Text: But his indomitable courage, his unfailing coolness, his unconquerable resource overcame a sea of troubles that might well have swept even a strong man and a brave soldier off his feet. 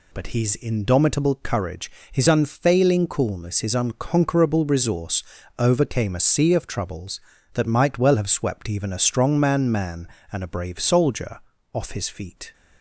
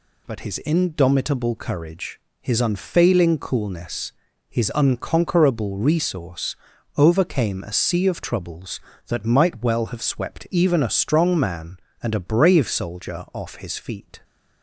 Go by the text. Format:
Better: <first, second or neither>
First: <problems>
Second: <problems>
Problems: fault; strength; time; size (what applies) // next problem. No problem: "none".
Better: second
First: pauses between "resource" and "overcame"; slight; at 5.2 s; 0.36 s long // says "man" twice; at 9.7 s // pauses between "soldier" and "off"; slight; at 11.4 s; 0.32 s long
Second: pauses between "resource" and "overcame"; at 6.5 s; 0.42 s long